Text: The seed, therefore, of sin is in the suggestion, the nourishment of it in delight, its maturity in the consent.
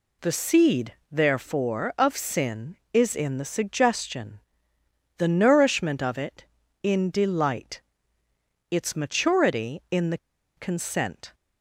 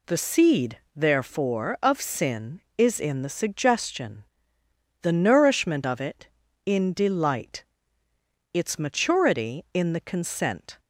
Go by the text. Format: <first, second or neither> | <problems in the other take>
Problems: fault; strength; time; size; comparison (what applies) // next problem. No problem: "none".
second | pauses between "the" and "consent"; at 10.1 s; 0.39 s long